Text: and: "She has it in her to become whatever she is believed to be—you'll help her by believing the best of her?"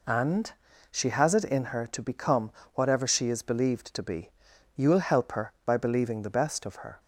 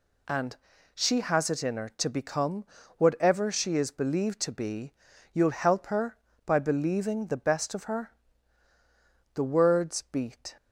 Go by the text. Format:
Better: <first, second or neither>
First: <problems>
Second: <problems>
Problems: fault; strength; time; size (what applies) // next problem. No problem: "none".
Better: first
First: pauses between "become" and "whatever"; slight; at 2.4 s; 0.24 s long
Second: pauses between "become" and "whatever"; slight; at 2.6 s; 0.32 s long // goes on to say "The words beat"; noticeable; from 9.3 s on; 1.2 s long